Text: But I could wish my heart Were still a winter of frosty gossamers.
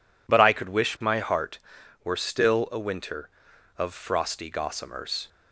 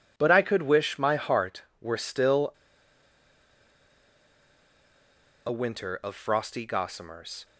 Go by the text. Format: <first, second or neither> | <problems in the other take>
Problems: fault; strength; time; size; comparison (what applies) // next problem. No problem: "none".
first | pauses between "still" and "a"; strong; at 2.5 s; 2.9 s long